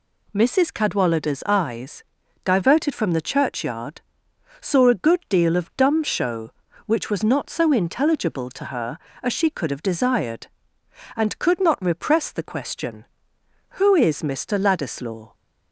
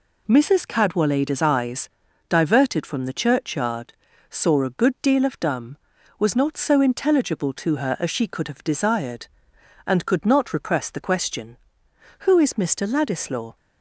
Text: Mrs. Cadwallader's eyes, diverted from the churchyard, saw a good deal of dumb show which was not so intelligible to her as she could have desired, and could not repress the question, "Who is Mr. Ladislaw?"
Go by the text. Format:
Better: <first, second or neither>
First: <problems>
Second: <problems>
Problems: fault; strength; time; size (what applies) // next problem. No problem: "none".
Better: first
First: none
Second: skips "show which"; at 5.9 s